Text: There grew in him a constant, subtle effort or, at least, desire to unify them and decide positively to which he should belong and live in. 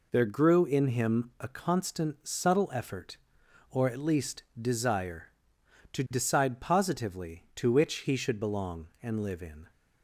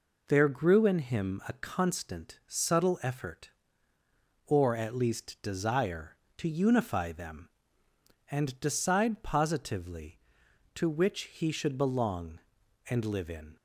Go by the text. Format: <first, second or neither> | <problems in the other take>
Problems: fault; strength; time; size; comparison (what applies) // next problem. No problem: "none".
second | skips "unify them and"; at 6.0 s